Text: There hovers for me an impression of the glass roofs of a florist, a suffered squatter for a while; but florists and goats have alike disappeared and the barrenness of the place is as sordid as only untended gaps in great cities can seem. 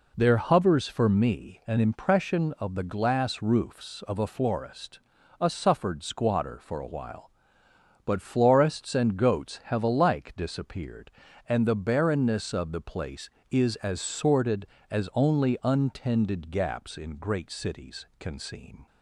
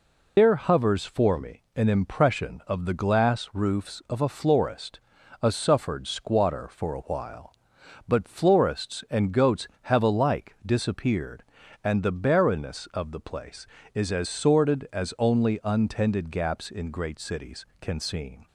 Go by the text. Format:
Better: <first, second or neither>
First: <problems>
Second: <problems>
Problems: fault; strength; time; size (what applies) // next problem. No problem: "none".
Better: first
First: none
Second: loses the start of "There"; at 0.3 s; 135 ms // pauses between "me" and "an"; slight; at 1.6 s; 0.16 s long